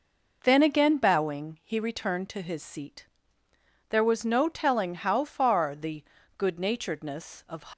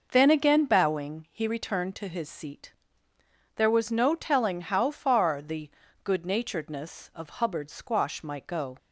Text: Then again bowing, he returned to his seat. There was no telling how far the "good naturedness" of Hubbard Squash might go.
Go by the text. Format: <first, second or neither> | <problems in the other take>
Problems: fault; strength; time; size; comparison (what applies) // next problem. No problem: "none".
second | pauses between "the" and "good"; slight; at 6.0 s; 0.36 s long; slight in the second // stops before "Hubbard Squash might go"; at 7.7 s